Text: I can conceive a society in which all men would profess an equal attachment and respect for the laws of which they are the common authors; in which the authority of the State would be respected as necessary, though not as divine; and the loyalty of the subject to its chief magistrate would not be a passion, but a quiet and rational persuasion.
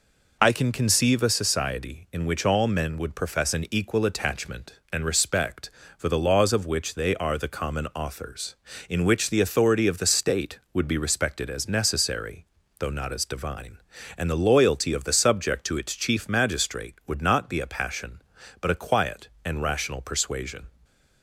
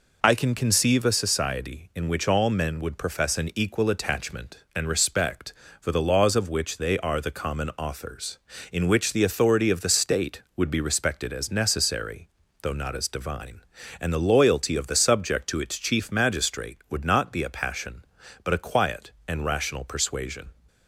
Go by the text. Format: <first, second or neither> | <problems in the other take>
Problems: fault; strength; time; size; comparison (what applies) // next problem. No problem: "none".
neither | none